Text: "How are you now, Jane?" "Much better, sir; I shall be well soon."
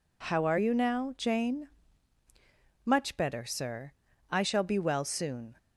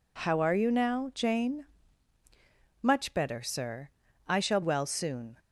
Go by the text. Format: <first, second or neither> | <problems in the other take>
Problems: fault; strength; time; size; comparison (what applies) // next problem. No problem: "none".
first | skips "be"; at 4.6 s